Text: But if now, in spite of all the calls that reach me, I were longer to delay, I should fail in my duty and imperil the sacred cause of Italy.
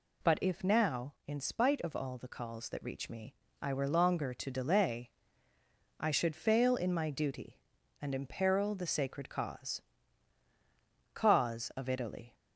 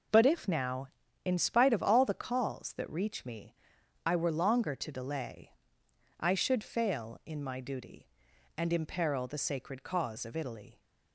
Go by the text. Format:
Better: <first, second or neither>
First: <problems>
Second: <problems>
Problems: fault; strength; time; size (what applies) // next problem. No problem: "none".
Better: second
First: says "cause" twice; at 11.1 s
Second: none